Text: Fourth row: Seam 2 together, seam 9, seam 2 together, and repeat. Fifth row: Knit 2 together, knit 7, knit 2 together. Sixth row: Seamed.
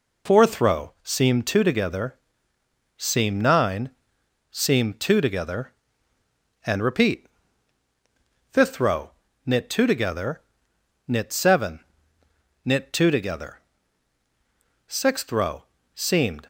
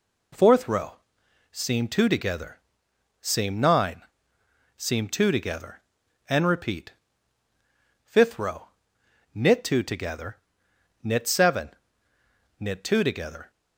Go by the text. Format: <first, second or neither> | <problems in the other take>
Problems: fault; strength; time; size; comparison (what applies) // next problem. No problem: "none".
first | stops before "Sixth row Seamed"; at 13.4 s